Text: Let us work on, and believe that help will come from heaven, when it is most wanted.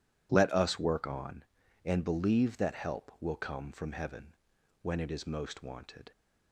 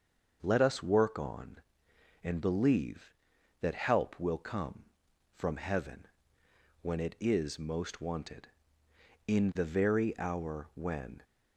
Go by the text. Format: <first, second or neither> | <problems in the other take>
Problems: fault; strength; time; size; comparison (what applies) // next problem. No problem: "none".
first | starts louder than the rest; until 1.4 s; 6.5 dB // goes on to say "In the very hour when"; strong; from 9.2 s on; 1.9 s long